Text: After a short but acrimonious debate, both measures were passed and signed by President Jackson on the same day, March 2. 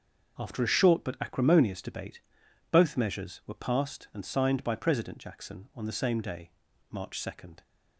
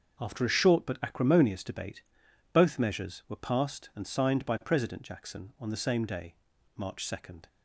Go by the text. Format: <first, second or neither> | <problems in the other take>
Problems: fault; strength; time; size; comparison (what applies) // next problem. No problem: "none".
neither | starts louder than the rest; the same in both